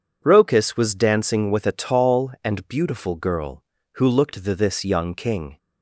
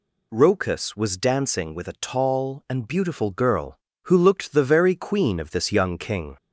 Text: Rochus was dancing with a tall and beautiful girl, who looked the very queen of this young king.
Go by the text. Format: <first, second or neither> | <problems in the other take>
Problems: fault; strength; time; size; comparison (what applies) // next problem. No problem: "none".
second | skips "very queen of"; at 4.5 s